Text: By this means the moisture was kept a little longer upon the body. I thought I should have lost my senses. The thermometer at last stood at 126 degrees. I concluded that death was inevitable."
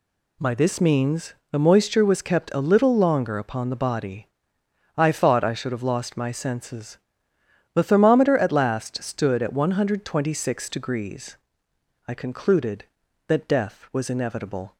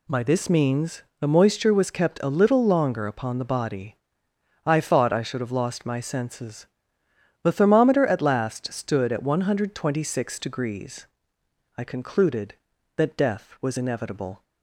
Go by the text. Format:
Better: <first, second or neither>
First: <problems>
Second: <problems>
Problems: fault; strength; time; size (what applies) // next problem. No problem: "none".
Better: neither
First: pauses between "means" and "the"; slight; at 1.3 s; 0.18 s long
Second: pauses between "means" and "the"; slight; at 1.0 s; 0.18 s long